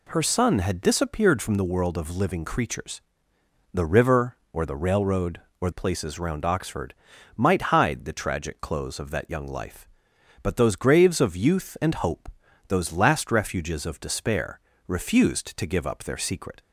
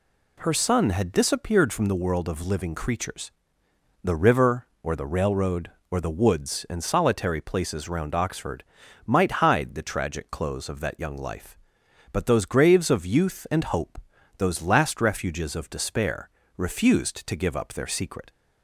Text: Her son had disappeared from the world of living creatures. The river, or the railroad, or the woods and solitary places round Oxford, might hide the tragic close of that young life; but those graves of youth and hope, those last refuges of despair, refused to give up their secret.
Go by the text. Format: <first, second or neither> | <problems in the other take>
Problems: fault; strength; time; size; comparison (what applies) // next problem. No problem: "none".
second | skips "the woods and solitary"; at 5.7 s